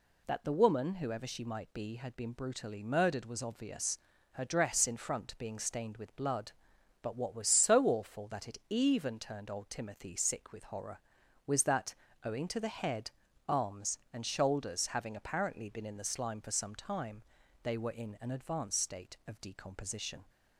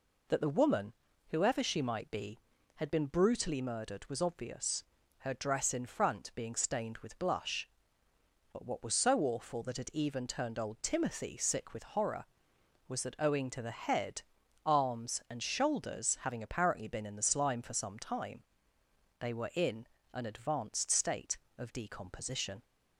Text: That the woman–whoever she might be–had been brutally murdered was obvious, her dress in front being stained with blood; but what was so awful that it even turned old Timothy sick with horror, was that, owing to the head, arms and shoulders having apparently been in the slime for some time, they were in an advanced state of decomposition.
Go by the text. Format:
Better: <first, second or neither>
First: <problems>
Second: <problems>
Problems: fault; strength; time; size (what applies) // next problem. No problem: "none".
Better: first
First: none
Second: says "blush" for "blood"; at 7.1 s // pauses between "in" and "an"; slight; at 19.8 s; 0.26 s long